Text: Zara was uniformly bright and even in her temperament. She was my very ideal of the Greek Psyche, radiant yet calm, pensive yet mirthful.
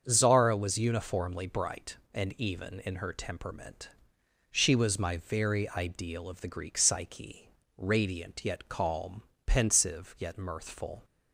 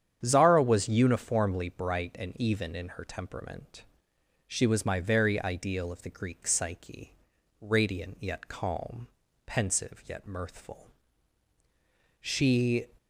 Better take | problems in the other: first | starts louder than the rest; strong; until 1.2 s; 8.5 dB; strong in the first // goes on to say "She"; noticeable; from 12.1 s on; 0.68 s long

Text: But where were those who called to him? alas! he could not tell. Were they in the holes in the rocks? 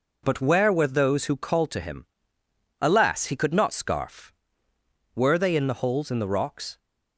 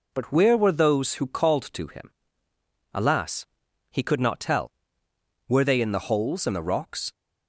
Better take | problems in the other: second | says "scarf" for "tell"; at 3.7 s

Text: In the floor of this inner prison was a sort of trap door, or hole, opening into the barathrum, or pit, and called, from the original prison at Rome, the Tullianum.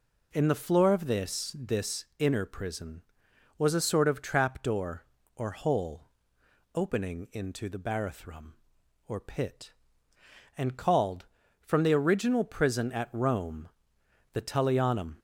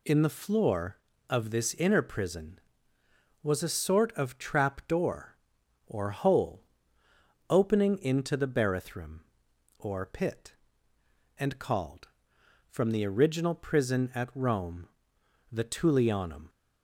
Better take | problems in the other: second | says "this" twice; at 1.5 s

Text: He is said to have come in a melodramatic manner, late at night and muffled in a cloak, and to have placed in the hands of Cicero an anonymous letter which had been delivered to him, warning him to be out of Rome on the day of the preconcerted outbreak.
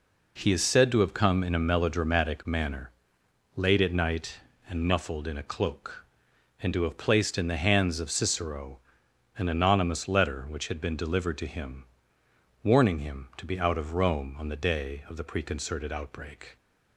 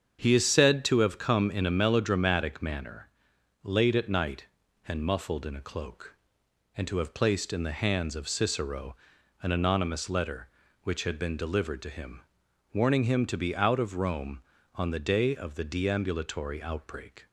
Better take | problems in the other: first | starts louder than the rest; strong; until 1.2 s; 7 dB // pauses between "Cicero" and "an"; noticeable; at 8.9 s; 0.48 s long; noticeable in the first // says "deambulatory" for "preconcerted"; at 15.6 s

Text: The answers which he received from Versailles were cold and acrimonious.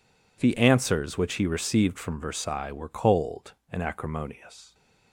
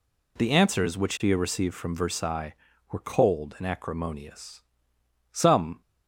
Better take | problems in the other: first | goes on to say "Some"; slight; from 5.3 s on; 0.48 s long

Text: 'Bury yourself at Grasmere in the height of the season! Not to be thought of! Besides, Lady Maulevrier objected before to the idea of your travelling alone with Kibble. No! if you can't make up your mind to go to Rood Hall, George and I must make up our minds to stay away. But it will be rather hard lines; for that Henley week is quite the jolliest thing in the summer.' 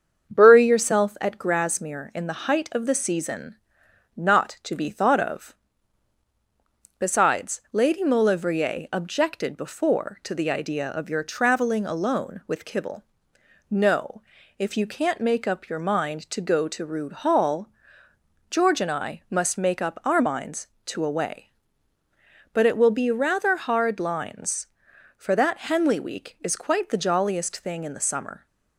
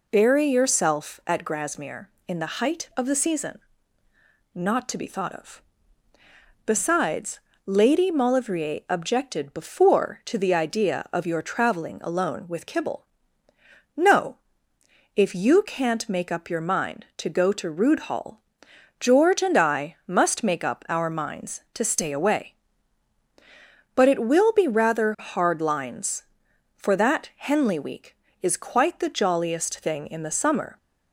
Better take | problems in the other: second | starts louder than the rest; until 1.3 s; 7 dB // skips "stay"; at 21.0 s

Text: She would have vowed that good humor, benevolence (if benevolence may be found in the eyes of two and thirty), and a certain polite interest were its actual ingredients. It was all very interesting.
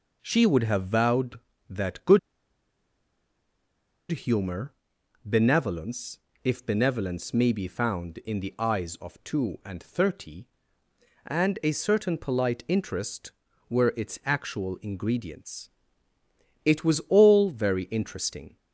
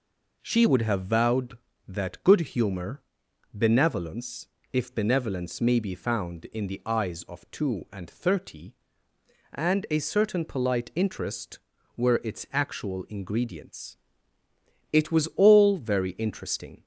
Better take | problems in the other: second | pauses between "good" and "humor"; strong; at 2.1 s; 1.9 s long

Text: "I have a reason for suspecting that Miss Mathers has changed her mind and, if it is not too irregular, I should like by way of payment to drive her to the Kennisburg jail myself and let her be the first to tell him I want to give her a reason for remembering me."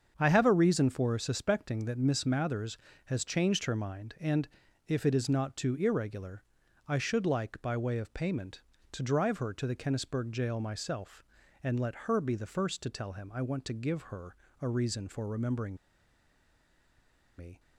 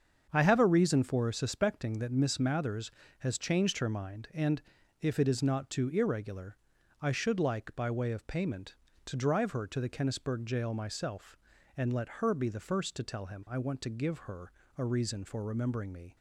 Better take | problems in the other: second | starts louder than the rest; strong; until 1.1 s; 7 dB; strong in the second // pauses between "her" and "a"; slight; at 14.3 s; 0.24 s long; slight in the second // pauses between "remembering" and "me"; strong; at 15.7 s; 1.6 s long

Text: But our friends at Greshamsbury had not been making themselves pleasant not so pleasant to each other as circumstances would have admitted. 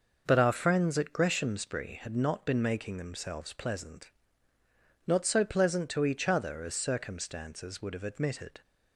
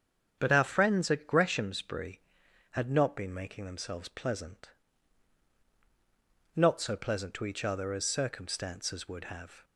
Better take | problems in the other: first | starts louder than the rest; strong; until 1.4 s; 8 dB // pauses between "pleasant" and "not"; strong; at 4.6 s; 1.8 s long; noticeable in the first // stops before "admitted"; at 9.6 s

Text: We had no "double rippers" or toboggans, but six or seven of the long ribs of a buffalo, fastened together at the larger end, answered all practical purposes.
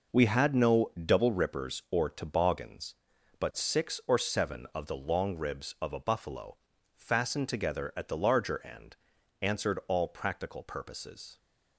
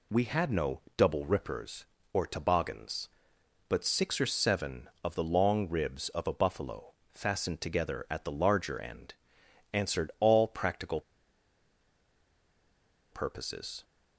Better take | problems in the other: first | pauses between "no" and "double"; slight; at 0.8 s; 0.18 s long // pauses between "practical" and "purposes"; strong; at 11.0 s; 2.1 s long

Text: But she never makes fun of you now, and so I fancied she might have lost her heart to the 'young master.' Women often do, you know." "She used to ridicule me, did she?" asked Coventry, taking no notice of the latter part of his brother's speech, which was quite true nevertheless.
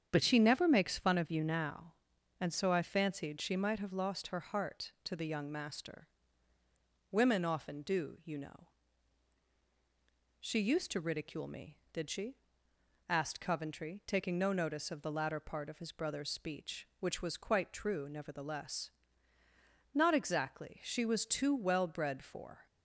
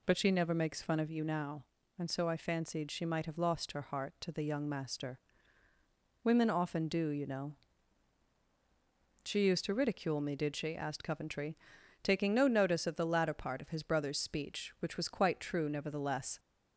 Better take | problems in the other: second | starts louder than the rest; strong; until 1.1 s; 8 dB // goes on to say "Not exactly she was too well bred for"; strong; from 19.9 s on; 2.7 s long

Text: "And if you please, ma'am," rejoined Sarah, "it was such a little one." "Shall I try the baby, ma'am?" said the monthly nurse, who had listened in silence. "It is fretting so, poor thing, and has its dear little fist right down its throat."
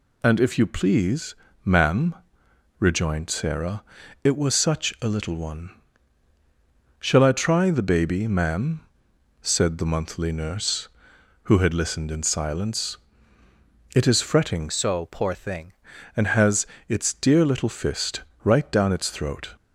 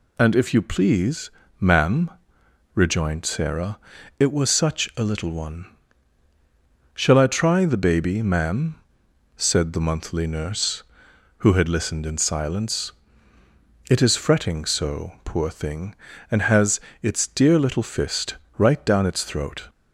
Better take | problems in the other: second | changes voice from "so" to "thing"; from 14.6 to 15.7 s; 1.1 s long // pauses between "has" and "its"; slight; at 16.6 s; 0.22 s long; slight in the second // pauses between "fist" and "right"; slight; at 18.2 s; 0.22 s long; slight in the second

